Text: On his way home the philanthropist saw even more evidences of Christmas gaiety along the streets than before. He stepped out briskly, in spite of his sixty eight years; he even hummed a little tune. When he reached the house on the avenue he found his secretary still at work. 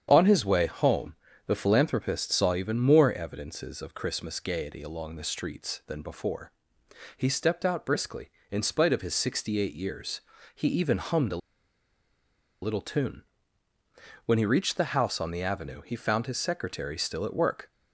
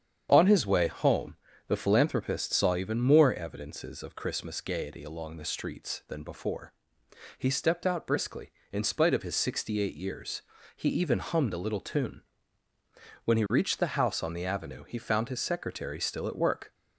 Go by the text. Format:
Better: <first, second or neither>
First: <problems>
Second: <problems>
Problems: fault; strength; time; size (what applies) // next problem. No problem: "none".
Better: second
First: starts louder than the rest; strong; until 1.1 s; 8.5 dB // pauses between "home" and "the"; slight; at 1.1 s; 0.32 s long // pauses between "a" and "little"; at 11.3 s; 1.2 s long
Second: starts louder than the rest; strong; until 1.3 s; 8.5 dB // pauses between "home" and "the"; slight; at 1.3 s; 0.32 s long